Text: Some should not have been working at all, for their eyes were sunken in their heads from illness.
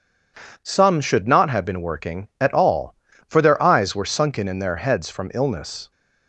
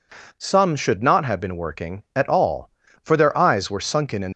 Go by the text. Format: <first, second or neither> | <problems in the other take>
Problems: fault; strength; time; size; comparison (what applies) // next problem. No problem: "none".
first | stops before "their heads from illness"; at 4.3 s